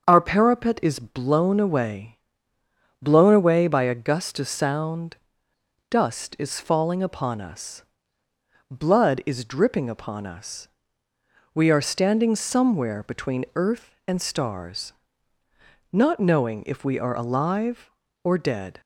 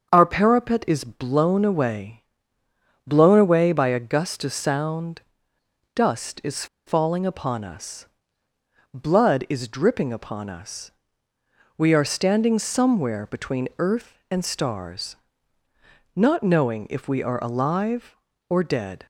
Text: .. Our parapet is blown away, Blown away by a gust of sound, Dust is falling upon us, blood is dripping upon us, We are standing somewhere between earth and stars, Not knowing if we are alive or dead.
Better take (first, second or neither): first